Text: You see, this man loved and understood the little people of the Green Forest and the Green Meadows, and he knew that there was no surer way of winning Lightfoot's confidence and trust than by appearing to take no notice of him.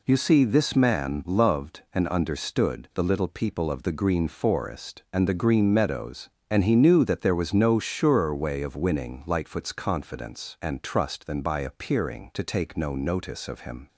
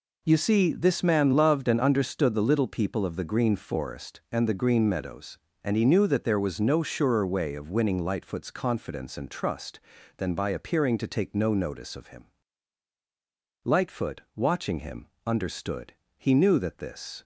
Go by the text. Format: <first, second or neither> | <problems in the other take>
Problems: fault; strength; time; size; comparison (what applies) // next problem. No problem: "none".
first | goes on to say "Lightfoot watching him understood He knew that this"; strong; from 13.6 s on; 3.6 s long